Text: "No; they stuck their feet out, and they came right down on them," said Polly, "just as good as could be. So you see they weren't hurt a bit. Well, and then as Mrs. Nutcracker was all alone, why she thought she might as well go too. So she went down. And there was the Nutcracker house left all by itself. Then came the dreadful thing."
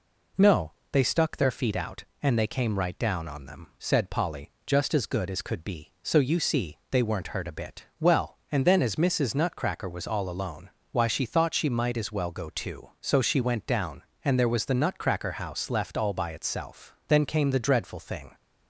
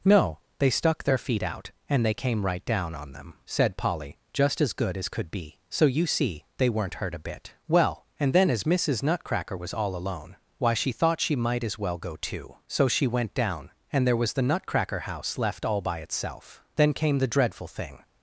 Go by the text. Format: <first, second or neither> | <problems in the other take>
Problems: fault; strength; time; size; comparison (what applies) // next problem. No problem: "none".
neither | none